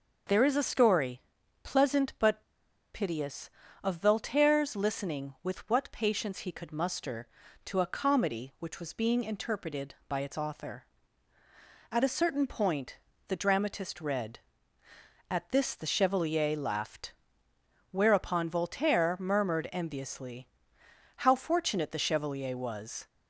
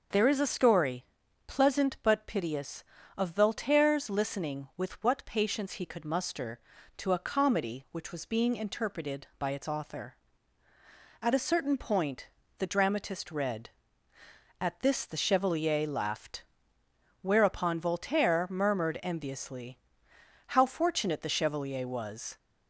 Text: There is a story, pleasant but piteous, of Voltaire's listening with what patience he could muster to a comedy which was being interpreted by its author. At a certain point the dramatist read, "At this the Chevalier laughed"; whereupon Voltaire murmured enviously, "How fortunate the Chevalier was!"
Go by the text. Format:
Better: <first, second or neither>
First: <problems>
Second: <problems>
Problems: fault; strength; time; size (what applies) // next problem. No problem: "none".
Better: second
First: starts louder than the rest; noticeable; until 1.7 s; 6 dB // pauses between "but" and "piteous"; noticeable; at 2.4 s; 0.52 s long // pauses between "point" and "the"; slight; at 12.9 s; 0.28 s long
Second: pauses between "point" and "the"; slight; at 12.2 s; 0.28 s long